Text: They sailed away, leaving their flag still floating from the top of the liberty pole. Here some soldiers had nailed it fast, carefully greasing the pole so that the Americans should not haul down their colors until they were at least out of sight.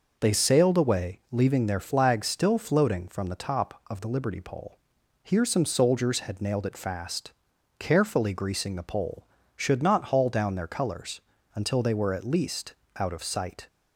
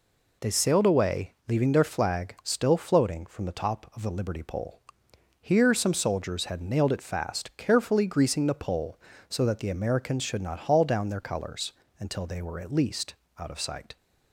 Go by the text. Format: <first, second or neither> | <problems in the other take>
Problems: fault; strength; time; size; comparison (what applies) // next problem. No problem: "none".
second | skips "so that the Americans"; at 9.3 s // pauses between "colors" and "until"; slight; at 11.1 s; 0.36 s long; slight in the second // pauses between "least" and "out"; slight; at 12.7 s; 0.24 s long; slight in the second